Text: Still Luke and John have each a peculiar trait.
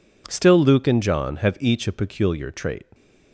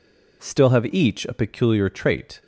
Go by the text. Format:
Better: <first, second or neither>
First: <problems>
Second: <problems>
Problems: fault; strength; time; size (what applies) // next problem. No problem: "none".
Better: first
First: none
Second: skips "Luke and John"; at 0.7 s